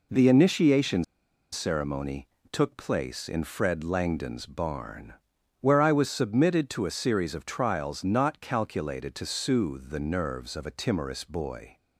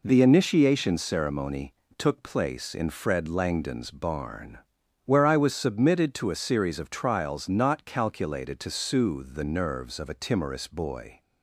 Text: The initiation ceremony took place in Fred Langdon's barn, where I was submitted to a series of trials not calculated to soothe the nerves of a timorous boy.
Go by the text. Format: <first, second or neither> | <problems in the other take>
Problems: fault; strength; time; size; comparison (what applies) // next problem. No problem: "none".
second | pauses between "initiation" and "ceremony"; noticeable; at 1.0 s; 0.49 s long // pauses between "ceremony" and "took"; slight; at 2.2 s; 0.22 s long; slight in the second